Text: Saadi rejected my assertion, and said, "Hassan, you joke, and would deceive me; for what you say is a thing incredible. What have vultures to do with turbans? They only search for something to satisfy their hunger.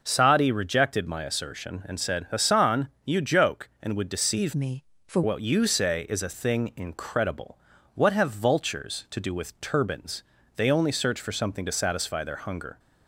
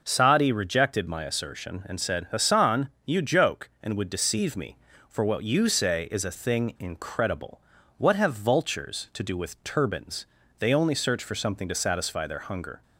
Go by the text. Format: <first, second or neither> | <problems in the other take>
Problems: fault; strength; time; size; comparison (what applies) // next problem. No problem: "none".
second | changes voice from "me" to "for"; from 4.5 to 5.2 s; 0.7 s long